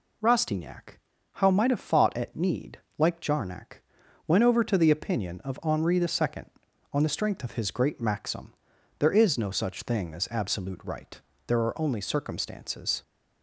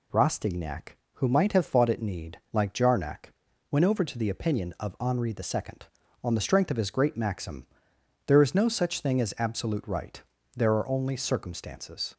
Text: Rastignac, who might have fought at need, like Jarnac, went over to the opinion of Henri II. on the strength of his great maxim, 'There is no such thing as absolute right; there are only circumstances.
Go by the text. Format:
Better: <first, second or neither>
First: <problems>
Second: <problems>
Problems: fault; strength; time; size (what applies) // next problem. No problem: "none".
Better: second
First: says "how" for "who"; at 1.3 s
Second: none